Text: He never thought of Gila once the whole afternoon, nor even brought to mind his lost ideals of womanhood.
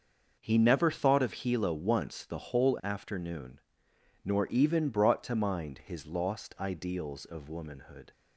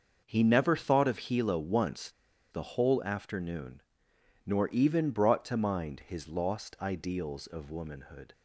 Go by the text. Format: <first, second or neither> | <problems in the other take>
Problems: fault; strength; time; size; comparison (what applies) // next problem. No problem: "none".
first | starts louder than the rest; until 1.3 s; 6 dB; also in the first // pauses between "once" and "the"; at 2.0 s; 0.41 s long